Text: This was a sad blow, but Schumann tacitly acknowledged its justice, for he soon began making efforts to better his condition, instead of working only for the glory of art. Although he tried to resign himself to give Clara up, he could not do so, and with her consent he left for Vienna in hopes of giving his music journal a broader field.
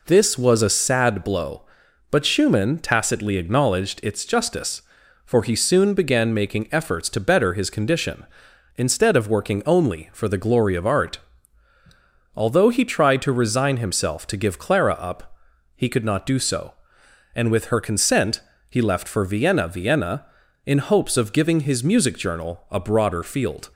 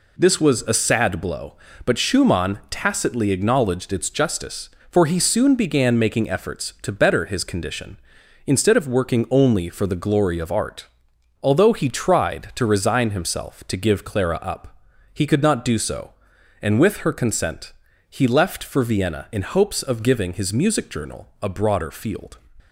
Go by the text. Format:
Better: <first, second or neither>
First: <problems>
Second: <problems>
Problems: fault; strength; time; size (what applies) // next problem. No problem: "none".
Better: second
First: pauses between "consent" and "he"; slight; at 18.4 s; 0.28 s long // says "Vienna" twice; at 19.6 s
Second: pauses between "consent" and "he"; slight; at 17.7 s; 0.36 s long